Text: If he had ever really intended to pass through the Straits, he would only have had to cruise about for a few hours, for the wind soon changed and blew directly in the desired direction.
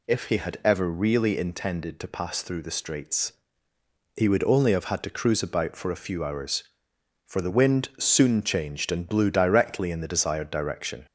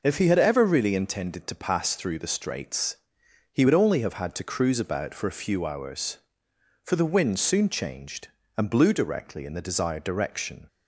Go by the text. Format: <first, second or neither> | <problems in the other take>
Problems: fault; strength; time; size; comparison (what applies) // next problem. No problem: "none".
neither | none